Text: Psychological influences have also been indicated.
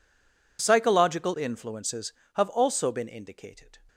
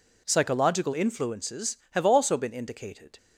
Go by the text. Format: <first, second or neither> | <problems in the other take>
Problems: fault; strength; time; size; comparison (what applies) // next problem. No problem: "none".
second | stays silent before the first word; slight; until 0.5 s; 0.5 s long